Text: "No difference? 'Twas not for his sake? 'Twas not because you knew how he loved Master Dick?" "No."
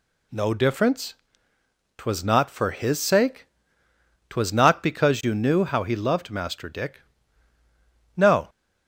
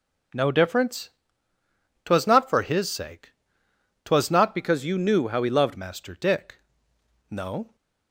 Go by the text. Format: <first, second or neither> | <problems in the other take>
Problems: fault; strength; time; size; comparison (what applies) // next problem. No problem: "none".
first | changes voice from "because" to "loved"; from 4.5 to 5.7 s; 1.2 s long